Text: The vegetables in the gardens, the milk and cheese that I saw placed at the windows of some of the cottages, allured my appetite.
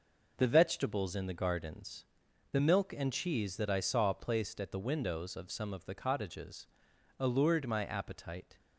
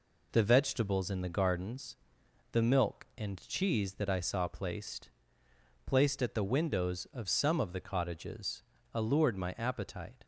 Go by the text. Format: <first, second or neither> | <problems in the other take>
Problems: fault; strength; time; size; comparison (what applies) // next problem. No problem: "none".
first | says "placed" twice; at 5.8 s